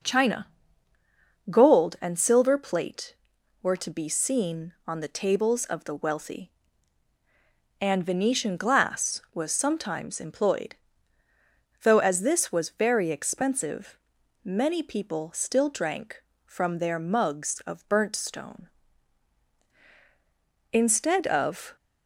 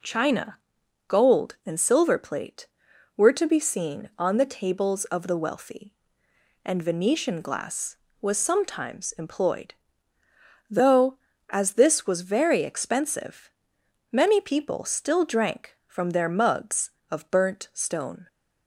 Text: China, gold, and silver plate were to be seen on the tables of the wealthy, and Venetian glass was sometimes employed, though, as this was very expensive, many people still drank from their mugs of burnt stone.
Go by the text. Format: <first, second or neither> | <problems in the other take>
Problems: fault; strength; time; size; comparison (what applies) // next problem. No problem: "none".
second | goes on to say "Instead of"; noticeable; from 20.7 s on; 1.0 s long